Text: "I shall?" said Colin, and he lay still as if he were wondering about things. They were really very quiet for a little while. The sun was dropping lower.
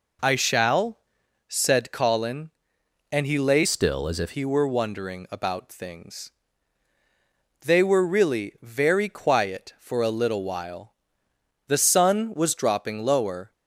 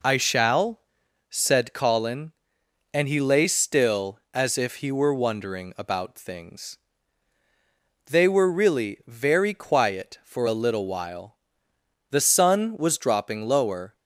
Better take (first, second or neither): second